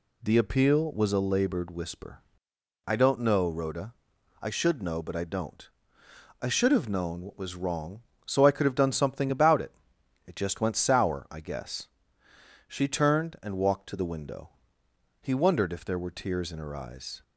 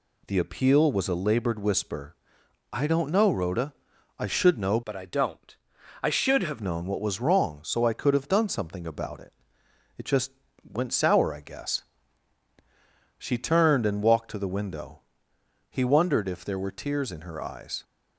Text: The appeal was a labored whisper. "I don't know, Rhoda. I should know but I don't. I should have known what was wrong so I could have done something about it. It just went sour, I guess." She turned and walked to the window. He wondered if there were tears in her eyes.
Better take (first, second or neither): first